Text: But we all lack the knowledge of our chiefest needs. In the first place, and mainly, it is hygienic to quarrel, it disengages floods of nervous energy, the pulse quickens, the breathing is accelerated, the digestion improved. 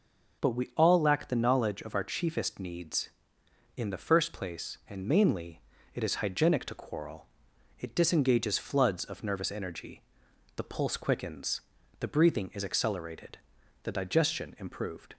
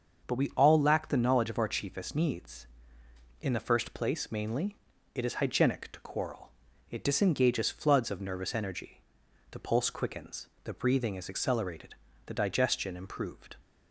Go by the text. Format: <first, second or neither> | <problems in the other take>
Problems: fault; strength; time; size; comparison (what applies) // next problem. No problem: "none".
first | starts louder than the rest; until 1.3 s; 6.5 dB; also in the first // skips "and"; at 4.3 s